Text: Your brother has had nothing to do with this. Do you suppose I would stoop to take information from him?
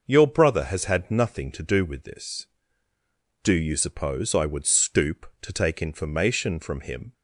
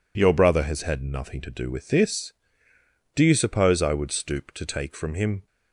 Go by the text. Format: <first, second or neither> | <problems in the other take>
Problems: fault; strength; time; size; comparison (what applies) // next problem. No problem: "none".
first | skips "information"; at 4.9 s